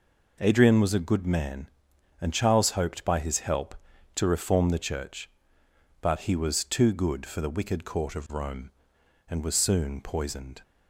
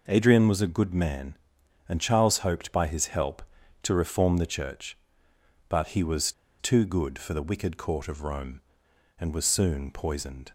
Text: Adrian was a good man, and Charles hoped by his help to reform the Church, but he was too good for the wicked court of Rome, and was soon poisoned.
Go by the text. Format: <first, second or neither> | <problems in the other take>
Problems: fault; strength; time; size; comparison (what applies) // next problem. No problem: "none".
first | pauses between "was" and "too"; slight; at 6.3 s; 0.28 s long